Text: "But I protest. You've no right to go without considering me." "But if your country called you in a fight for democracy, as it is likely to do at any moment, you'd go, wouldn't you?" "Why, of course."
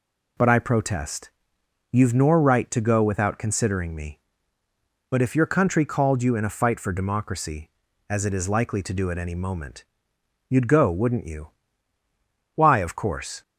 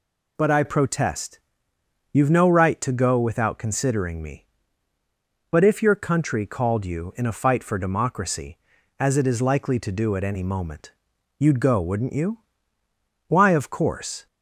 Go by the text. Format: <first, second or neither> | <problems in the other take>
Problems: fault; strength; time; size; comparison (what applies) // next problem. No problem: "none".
second | says "nor" for "no"; at 2.1 s